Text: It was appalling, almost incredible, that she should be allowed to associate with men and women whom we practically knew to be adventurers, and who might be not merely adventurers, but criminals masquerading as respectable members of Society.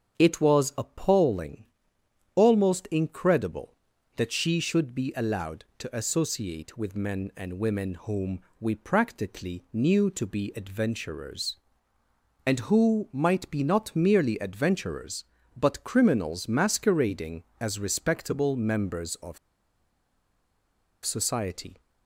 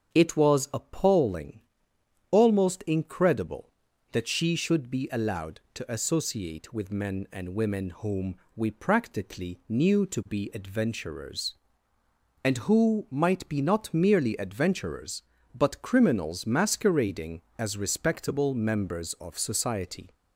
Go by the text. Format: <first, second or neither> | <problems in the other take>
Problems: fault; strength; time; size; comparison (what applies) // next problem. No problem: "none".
second | starts louder than the rest; strong; until 1.2 s; 8 dB; strong in the second // pauses between "whom" and "we"; slight; at 8.3 s; 0.22 s long; slight in the second // pauses between "of" and "Society"; strong; at 19.3 s; 1.6 s long